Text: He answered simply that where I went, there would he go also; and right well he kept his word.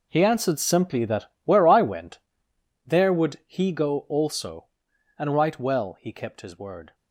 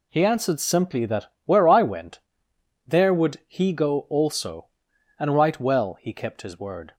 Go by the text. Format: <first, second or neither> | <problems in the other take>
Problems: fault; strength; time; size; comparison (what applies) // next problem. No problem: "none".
second | gets quieter; strong; throughout; 16 dB // pauses between "that" and "where"; slight; at 1.2 s; 0.18 s long; slight in the second